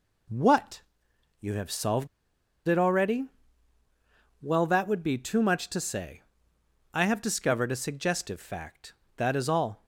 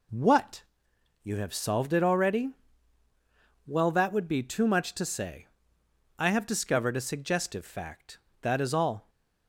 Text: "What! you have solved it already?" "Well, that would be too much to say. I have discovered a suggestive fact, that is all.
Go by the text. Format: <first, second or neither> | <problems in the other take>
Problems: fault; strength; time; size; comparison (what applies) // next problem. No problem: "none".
second | pauses between "solved" and "it"; noticeable; at 2.0 s; 0.60 s long